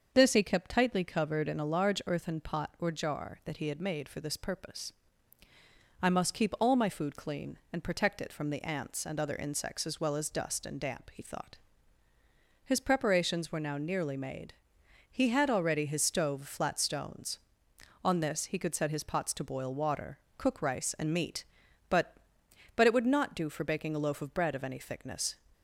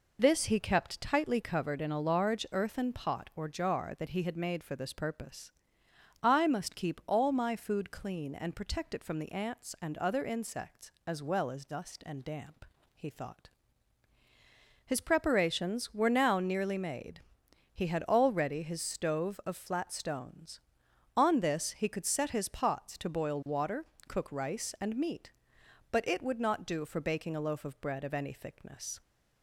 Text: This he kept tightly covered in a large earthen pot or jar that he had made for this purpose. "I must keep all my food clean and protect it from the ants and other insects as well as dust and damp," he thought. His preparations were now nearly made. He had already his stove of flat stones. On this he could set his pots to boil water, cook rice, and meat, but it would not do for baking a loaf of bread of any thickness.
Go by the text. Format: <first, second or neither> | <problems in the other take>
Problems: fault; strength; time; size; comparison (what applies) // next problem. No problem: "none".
second | starts louder than the rest; until 1.1 s; 6.5 dB // says "but" twice; at 22.7 s